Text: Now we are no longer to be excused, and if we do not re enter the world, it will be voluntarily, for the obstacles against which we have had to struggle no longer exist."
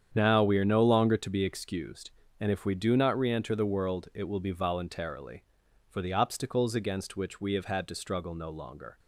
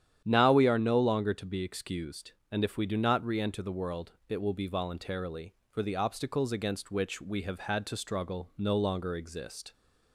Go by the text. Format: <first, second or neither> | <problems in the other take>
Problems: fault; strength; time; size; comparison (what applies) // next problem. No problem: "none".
second | starts louder than the rest; strong; until 1.1 s; 8.5 dB; strong in the second // stops before "exist"; at 8.9 s